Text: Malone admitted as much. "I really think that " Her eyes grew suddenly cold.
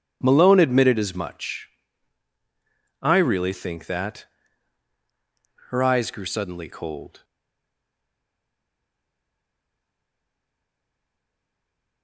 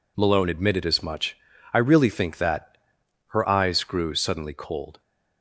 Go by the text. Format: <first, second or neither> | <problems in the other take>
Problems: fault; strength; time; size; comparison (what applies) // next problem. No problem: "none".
second | starts louder than the rest; strong; until 1.2 s; 8 dB // stays silent after the last word; strong; from 7.2 s on; 4.8 s long